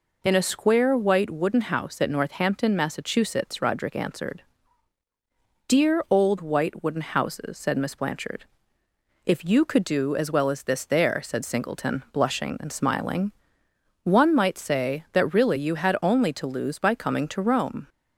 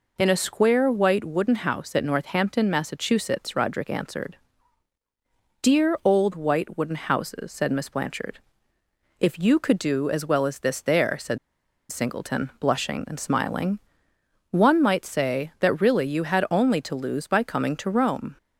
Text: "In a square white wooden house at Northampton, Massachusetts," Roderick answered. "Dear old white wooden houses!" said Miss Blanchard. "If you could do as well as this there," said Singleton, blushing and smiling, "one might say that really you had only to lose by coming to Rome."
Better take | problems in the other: first | pauses between "said" and "Singleton"; noticeable; at 11.3 s; 0.52 s long

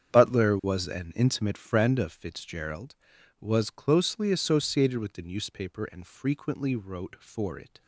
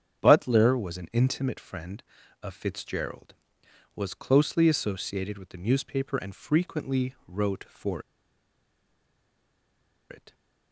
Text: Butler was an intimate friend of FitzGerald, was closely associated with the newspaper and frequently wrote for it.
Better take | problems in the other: first | starts louder than the rest; strong; until 1.2 s; 8 dB; strong in the first // pauses between "for" and "it"; strong; at 8.0 s; 2.0 s long

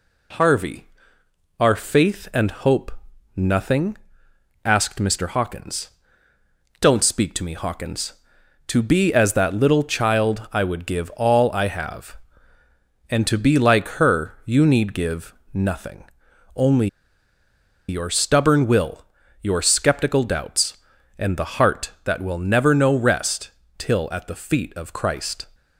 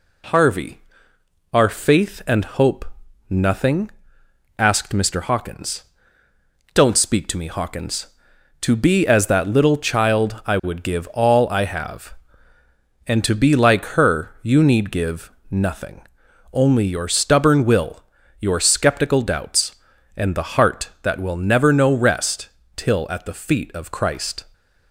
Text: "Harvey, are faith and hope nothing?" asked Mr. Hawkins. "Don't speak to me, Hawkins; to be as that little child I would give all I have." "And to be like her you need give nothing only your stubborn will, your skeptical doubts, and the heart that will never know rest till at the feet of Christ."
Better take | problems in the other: second | pauses between "hope" and "nothing"; noticeable; at 2.8 s; 0.46 s long; noticeable in the second // pauses between "give" and "nothing"; slight; at 15.3 s; 0.18 s long; slight in the second // pauses between "nothing" and "only"; noticeable; at 16.0 s; 0.50 s long; noticeable in the second // pauses between "only" and "your"; at 16.8 s; 1.0 s long // pauses between "rest" and "till"; slight; at 23.5 s; 0.28 s long; slight in the second

